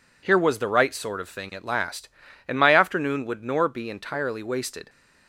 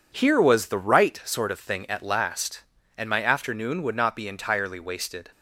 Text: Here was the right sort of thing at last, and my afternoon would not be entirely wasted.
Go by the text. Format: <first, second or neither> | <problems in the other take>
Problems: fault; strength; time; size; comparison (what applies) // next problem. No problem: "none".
second | says "nor" for "not"; at 3.4 s